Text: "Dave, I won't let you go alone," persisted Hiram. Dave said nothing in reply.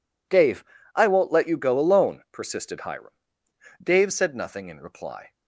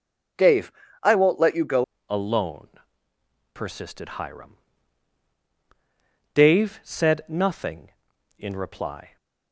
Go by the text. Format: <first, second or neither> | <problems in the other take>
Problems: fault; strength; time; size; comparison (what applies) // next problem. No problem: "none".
first | starts louder than the rest; strong; until 1.7 s; 7.5 dB // changes voice at "alone"; from 2.0 s on; 7.1 s long